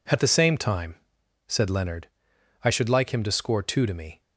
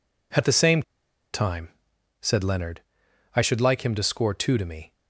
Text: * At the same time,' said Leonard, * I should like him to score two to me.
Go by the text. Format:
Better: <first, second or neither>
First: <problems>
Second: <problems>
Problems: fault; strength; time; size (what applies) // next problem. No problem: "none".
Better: first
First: none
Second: pauses between "same" and "time"; noticeable; at 0.8 s; 0.51 s long